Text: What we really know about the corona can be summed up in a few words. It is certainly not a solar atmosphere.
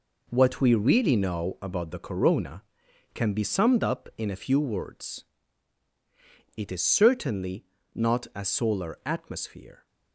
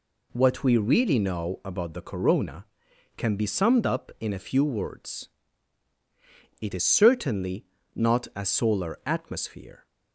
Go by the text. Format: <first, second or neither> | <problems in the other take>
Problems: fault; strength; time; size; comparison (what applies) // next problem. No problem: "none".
second | gets quieter; strong; throughout; 8.5 dB // pauses between "certainly" and "not"; slight; at 7.6 s; 0.30 s long; slight in the second